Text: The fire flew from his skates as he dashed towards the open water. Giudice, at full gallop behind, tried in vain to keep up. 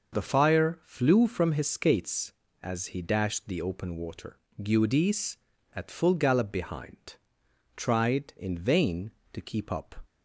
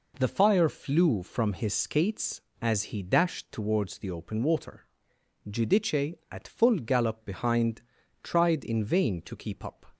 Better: second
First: starts louder than the rest; noticeable; until 1.2 s; 6 dB // skips "towards"; at 3.4 s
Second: none

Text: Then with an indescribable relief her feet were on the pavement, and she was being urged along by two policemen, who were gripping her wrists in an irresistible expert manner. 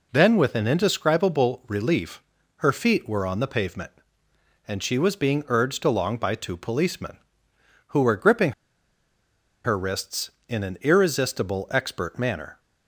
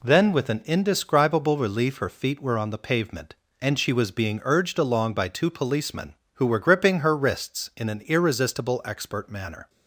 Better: second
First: pauses between "relief" and "her"; slight; at 2.2 s; 0.36 s long // pauses between "gripping" and "her"; at 8.5 s; 1.1 s long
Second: none

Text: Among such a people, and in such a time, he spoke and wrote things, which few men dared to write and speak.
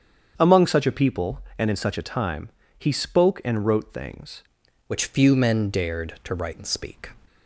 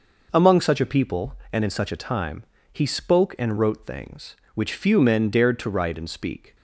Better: second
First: starts louder than the rest; strong; until 1.3 s; 7.5 dB // changes voice at "which"; from 4.8 s on; 2.2 s long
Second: none

